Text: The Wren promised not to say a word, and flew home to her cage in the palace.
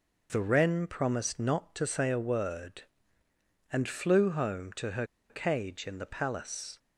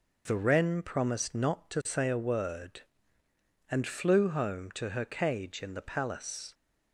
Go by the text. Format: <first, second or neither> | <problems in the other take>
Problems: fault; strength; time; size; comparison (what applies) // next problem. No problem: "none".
second | pauses between "her" and "cage"; slight; at 5.0 s; 0.24 s long